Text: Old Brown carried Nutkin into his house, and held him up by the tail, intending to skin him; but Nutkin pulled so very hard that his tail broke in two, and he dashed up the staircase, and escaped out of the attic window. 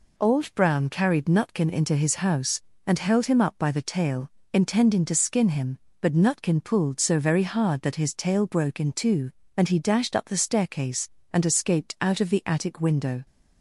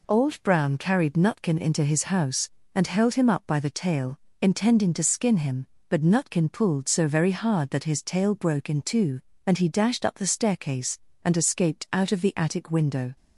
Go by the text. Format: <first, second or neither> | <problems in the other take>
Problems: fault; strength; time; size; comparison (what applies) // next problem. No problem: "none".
neither | none